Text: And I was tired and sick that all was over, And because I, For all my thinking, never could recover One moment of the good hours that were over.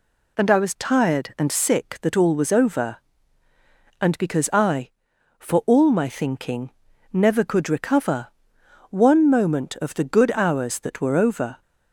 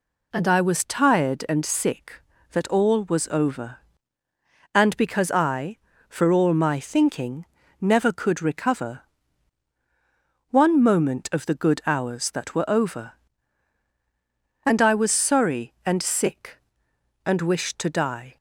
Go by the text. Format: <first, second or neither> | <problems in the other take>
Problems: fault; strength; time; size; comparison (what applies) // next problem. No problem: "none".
first | pauses between "recover" and "One"; strong; at 9.0 s; 1.4 s long; noticeable in the first // goes on to say "And I was sorry and sick and wished to die"; strong; from 14.6 s on; 3.7 s long